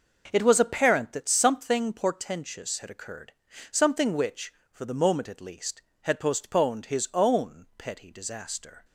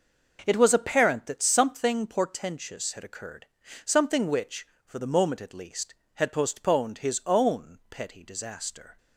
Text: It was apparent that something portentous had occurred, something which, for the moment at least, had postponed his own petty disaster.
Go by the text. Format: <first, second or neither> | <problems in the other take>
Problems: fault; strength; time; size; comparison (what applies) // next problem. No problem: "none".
neither | none